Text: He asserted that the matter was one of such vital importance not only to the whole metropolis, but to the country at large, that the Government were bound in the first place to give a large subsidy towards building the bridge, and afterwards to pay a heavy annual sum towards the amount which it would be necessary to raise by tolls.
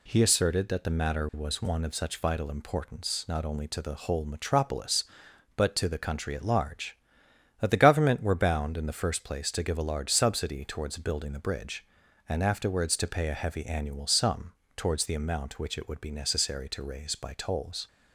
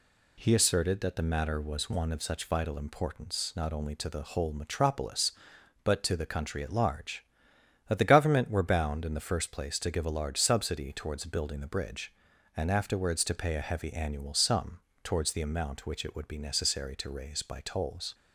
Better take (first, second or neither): neither